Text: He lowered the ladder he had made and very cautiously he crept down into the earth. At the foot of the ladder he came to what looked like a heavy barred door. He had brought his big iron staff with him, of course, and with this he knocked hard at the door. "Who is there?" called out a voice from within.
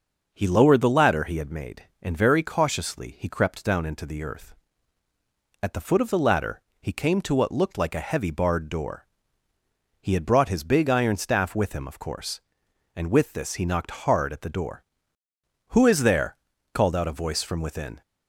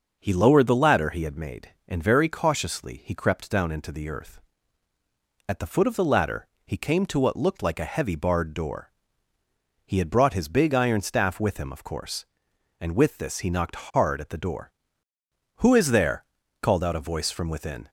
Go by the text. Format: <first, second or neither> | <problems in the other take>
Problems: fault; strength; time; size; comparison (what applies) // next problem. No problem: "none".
neither | starts louder than the rest; noticeable; the same in both // pauses between "ladder" and "he"; slight; the same in both